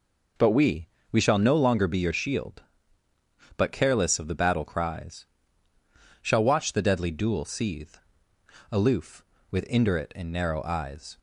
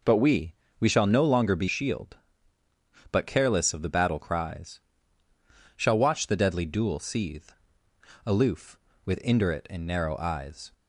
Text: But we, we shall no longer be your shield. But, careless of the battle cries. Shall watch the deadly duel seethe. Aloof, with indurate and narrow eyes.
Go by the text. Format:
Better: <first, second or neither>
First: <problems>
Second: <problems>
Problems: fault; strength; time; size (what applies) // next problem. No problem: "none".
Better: first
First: none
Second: skips "your"; at 1.6 s